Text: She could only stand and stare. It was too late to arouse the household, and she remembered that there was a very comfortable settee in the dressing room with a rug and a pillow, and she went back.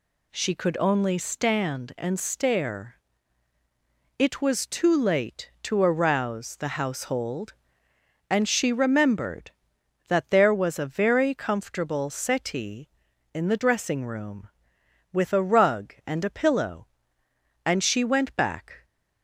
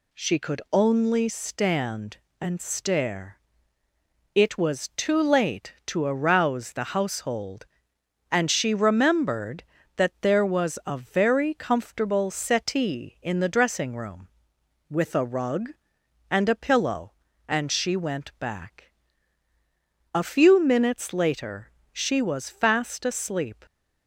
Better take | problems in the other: first | goes on to say "A few minutes later she was fast asleep"; strong; from 20.1 s on; 3.5 s long

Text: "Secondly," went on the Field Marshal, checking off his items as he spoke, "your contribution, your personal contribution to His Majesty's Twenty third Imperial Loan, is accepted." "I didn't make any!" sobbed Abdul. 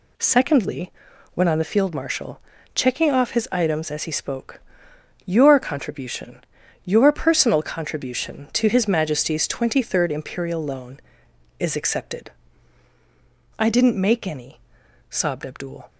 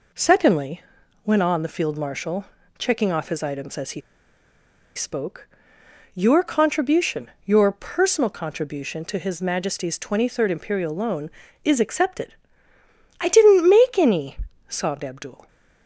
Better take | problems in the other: first | pauses between "he" and "spoke"; noticeable; at 4.0 s; 0.95 s long

